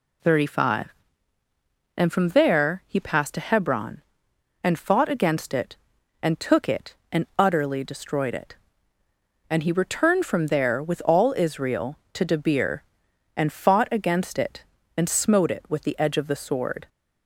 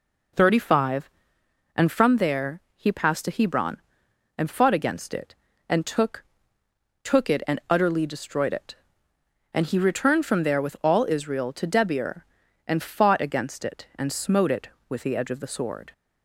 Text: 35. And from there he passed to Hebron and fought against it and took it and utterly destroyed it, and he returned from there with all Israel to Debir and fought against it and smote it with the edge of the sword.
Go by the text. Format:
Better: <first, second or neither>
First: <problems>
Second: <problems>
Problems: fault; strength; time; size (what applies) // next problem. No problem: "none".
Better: first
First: none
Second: says "took" twice; at 7.0 s